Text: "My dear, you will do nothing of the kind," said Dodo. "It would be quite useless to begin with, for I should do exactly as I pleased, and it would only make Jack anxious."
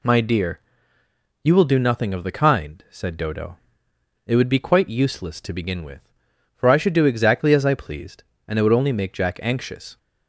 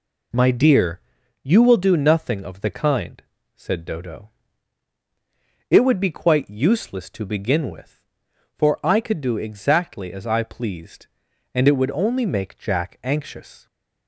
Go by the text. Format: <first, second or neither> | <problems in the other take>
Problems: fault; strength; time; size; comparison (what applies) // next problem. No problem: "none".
first | says "could" for "should"; at 9.0 s